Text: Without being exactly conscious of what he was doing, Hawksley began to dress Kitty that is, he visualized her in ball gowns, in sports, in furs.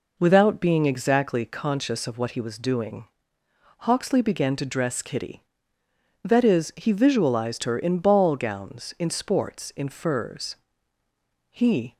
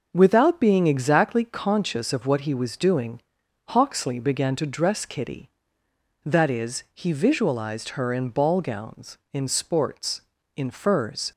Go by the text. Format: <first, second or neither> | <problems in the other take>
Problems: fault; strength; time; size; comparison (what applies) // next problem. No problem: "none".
second | goes on to say "He"; slight; from 11.4 s on; 0.48 s long